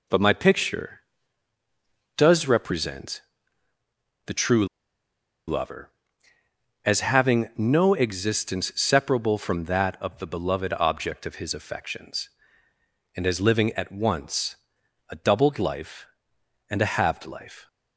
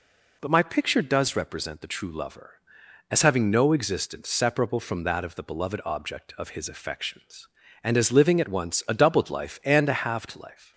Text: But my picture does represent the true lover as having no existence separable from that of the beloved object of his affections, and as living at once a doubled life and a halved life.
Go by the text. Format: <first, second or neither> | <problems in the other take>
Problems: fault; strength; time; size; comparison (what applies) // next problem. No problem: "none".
second | pauses between "represent" and "the"; at 3.2 s; 1.0 s long // pauses between "true" and "lover"; noticeable; at 4.6 s; 0.82 s long // pauses between "once" and "a"; noticeable; at 14.5 s; 0.54 s long